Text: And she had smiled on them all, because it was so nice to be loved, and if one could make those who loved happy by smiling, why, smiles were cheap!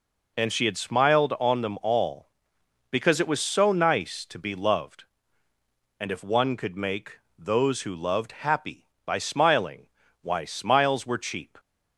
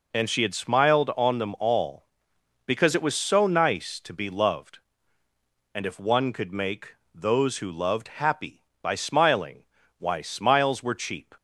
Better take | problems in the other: neither | pauses between "make" and "those"; slight; the same in both

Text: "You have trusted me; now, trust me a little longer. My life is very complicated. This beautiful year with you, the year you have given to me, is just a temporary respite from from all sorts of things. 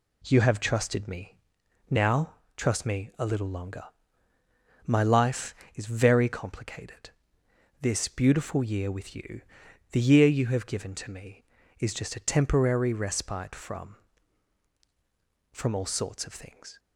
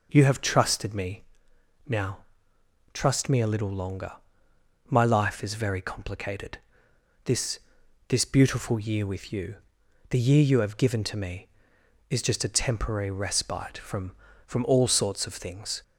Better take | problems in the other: first | says "This" twice; at 8.0 s

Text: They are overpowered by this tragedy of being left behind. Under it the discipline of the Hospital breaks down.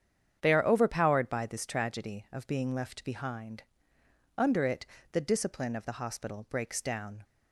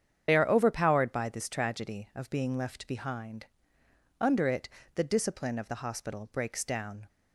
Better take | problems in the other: first | loses the start of "They"; at 0.2 s; 35 ms // starts louder than the rest; strong; until 1.2 s; 8.5 dB; strong in the first // pauses between "it" and "the"; slight; at 4.6 s; 0.26 s long; slight in the first

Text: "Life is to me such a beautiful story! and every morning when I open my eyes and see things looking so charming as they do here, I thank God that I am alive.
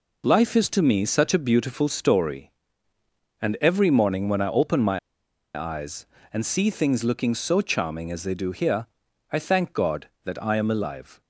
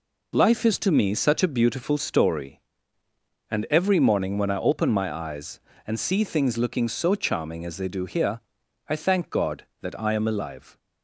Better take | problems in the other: second | pauses between "my" and "eyes"; noticeable; at 4.9 s; 0.55 s long

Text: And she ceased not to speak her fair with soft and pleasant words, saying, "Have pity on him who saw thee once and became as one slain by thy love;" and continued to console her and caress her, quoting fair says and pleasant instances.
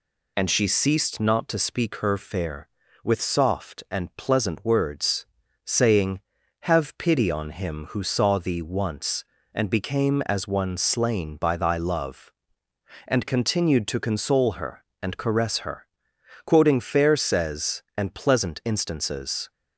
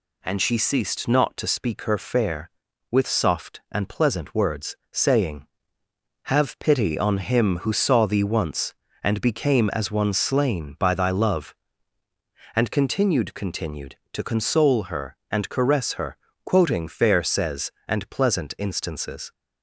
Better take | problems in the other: first | says "continued" twice; at 13.3 s

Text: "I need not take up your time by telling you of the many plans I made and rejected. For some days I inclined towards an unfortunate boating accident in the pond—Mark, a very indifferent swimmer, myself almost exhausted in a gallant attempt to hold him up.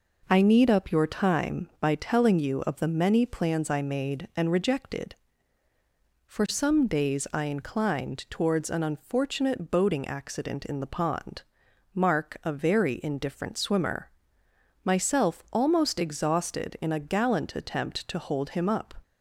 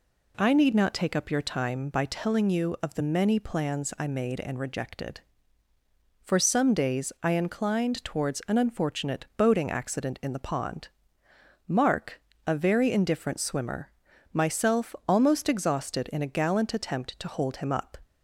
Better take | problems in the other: second | skips "not take"; at 0.7 s

